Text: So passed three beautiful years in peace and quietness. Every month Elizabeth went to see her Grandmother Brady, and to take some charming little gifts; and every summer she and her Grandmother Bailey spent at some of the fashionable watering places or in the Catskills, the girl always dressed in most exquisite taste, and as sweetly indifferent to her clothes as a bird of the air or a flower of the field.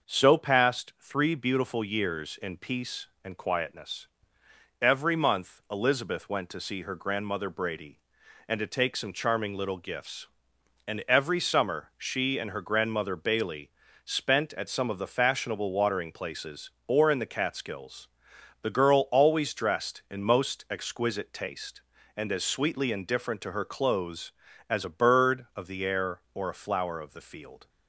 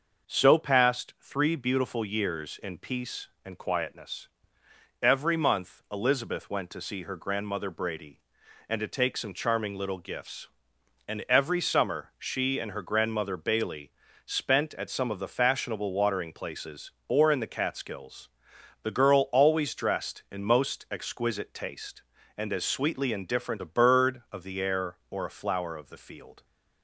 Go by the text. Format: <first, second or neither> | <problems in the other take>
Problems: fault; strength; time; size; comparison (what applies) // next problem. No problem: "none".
first | starts louder than the rest; until 1.3 s; 6 dB; noticeable in the first // pauses between "Bailey" and "spent"; slight; at 13.9 s; 0.34 s long; slight in the first // skips "to her clothes as"; at 23.6 s